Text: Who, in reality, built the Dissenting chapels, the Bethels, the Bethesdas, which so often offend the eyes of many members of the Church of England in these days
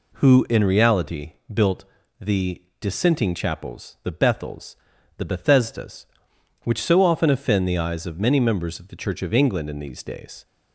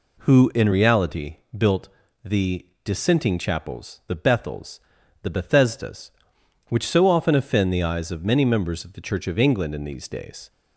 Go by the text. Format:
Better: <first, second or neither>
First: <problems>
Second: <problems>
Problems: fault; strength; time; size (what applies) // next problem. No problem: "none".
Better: neither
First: pauses between "built" and "the"; slight; at 1.8 s; 0.36 s long // pauses between "the" and "Dissenting"; slight; at 2.6 s; 0.18 s long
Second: pauses between "built" and "the"; slight; at 1.8 s; 0.36 s long // pauses between "the" and "Dissenting"; slight; at 2.6 s; 0.18 s long